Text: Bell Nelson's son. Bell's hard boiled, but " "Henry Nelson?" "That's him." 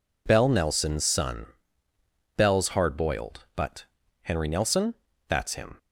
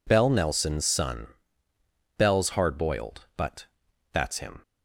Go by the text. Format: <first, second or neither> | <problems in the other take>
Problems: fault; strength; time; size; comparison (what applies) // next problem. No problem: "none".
first | skips "Henry Nelson"; at 4.0 s